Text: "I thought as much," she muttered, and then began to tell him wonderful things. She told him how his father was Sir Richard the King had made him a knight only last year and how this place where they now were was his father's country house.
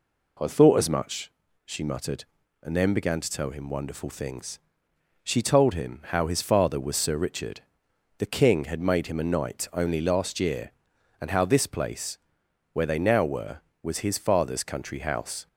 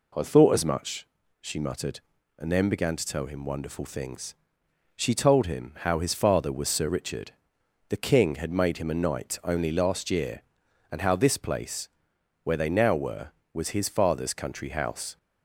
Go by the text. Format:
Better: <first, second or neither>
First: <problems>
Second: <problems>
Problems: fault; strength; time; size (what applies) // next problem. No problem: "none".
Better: neither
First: pauses between "Richard" and "the"; noticeable; at 7.6 s; 0.56 s long // pauses between "place" and "where"; noticeable; at 12.1 s; 0.54 s long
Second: pauses between "Richard" and "the"; noticeable; at 7.3 s; 0.56 s long // pauses between "place" and "where"; noticeable; at 11.8 s; 0.54 s long